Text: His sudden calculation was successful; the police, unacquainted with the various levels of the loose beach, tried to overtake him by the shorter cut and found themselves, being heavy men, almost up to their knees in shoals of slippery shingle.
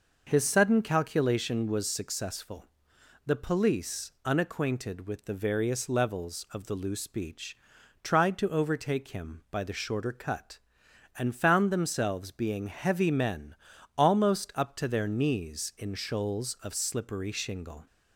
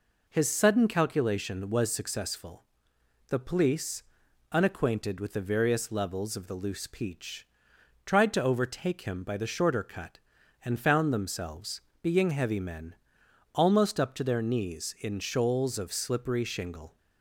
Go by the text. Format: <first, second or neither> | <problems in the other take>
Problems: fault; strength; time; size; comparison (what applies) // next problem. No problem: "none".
first | says "peach" for "beach"; at 6.8 s